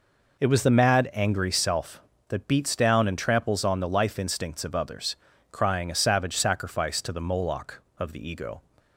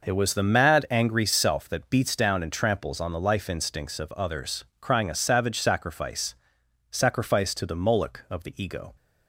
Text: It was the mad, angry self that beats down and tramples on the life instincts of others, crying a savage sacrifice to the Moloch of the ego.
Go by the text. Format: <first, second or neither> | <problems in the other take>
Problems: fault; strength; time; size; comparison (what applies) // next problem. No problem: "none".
first | says "sacrifice" twice; at 6.8 s